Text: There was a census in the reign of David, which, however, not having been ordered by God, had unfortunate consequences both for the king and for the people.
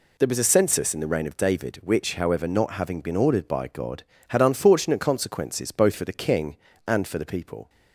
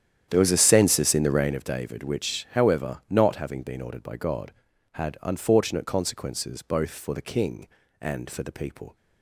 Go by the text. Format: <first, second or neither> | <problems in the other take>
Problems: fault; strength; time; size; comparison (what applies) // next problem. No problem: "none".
first | starts louder than the rest; strong; until 1.6 s; 9.5 dB